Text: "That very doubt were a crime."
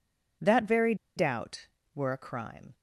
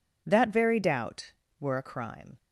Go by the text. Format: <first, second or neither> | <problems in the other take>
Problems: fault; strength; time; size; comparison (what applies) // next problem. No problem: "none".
second | pauses between "very" and "doubt"; slight; at 0.9 s; 0.21 s long